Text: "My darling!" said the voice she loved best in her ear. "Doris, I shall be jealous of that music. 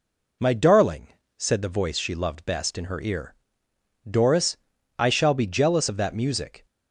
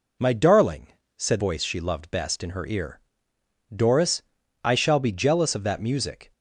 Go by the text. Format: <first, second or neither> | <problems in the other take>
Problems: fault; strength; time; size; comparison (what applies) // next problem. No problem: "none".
first | skips "the"; at 1.4 s